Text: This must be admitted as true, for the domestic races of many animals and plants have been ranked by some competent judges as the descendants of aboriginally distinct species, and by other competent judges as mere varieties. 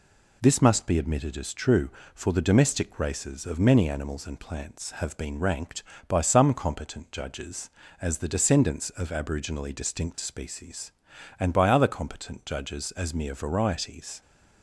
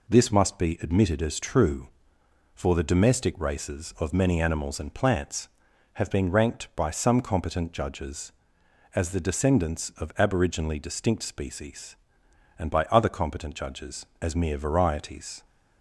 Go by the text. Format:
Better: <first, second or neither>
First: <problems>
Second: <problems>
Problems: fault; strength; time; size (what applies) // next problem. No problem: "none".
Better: neither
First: none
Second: none